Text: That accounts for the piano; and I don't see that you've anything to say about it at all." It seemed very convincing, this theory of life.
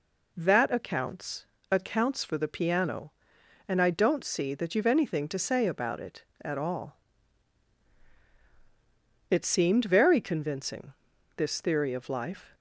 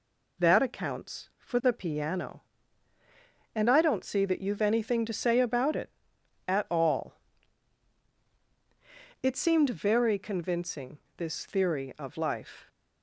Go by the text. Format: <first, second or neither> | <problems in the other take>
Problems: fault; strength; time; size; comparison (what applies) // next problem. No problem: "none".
second | says "accounts" twice; at 1.7 s